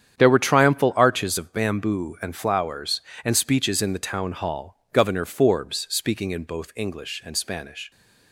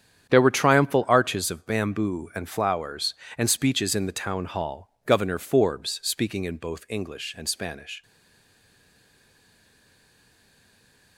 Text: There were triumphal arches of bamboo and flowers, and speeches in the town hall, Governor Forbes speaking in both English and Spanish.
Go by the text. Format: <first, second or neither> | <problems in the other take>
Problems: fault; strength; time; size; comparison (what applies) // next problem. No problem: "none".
first | starts louder than the rest; strong; until 1.3 s; 9 dB; strong in the first // stays silent after the last word; strong; from 8.0 s on; 3.1 s long